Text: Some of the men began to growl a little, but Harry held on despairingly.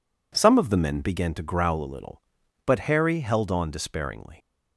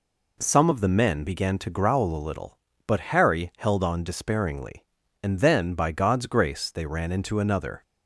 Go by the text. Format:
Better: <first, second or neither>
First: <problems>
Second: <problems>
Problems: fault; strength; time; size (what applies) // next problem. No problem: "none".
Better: first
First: none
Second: goes on to say "And then by God's grace they ran into another"; strong; from 5.2 s on; 2.6 s long